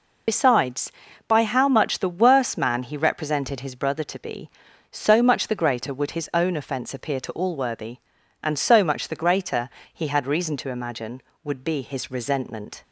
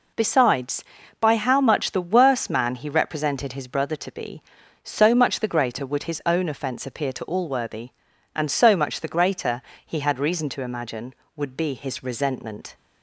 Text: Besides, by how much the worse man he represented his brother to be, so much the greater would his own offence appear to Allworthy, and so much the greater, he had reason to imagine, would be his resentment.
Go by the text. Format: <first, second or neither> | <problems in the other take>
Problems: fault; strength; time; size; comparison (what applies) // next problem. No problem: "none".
second | loses the start of "Besides"; at 0.2 s; 55 ms